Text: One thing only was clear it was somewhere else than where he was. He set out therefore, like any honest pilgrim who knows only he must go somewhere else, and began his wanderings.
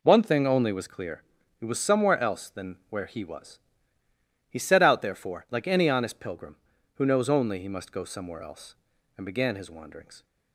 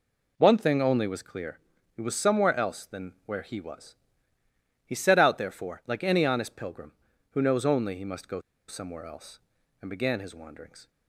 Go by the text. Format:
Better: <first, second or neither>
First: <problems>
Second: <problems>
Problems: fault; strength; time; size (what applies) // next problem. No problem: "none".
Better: first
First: pauses between "clear" and "it"; slight; at 1.2 s; 0.36 s long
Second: pauses between "clear" and "it"; slight; at 1.5 s; 0.36 s long // pauses between "go" and "somewhere"; slight; at 8.4 s; 0.27 s long